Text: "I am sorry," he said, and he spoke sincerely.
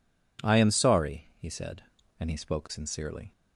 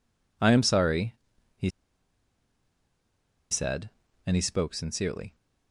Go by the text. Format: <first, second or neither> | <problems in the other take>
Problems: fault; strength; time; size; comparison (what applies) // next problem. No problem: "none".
first | pauses between "he" and "said"; strong; at 1.6 s; 1.8 s long